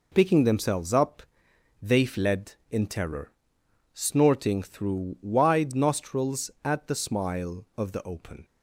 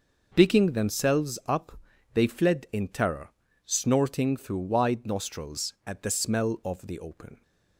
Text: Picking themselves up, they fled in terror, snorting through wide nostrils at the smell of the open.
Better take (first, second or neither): second